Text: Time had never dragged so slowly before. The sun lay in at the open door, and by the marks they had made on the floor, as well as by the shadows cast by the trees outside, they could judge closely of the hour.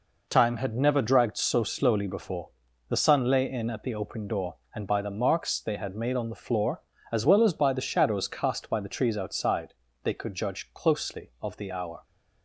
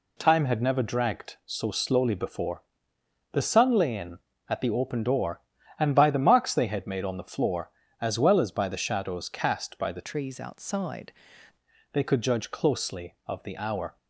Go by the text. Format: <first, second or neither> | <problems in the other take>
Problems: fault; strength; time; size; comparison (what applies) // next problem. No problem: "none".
first | changes voice from "trees" to "outside"; from 10.0 to 11.1 s; 1.1 s long